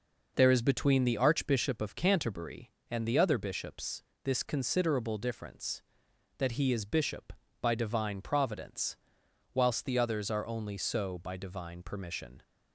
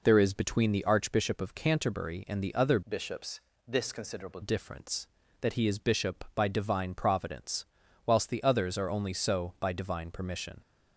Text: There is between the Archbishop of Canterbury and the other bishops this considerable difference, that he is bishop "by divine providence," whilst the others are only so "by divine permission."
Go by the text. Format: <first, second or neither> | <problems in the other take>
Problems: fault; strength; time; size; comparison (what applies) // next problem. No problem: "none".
first | changes voice from "bishops" to "considerable"; from 2.8 to 4.3 s; 1.5 s long // pauses between "bishops" and "this"; slight; at 3.4 s; 0.26 s long; slight in the first